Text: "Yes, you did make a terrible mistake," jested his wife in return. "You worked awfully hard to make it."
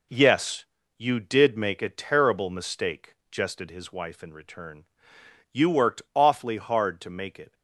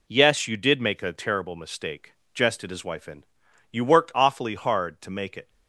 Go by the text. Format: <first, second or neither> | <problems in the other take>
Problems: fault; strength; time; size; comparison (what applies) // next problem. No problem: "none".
first | skips "return"; at 3.4 s